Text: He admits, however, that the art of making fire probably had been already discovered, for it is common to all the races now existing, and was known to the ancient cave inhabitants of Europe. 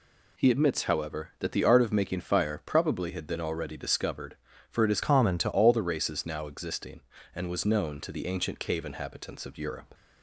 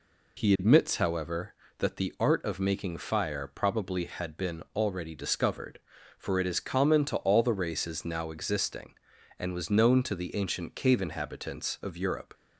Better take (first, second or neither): second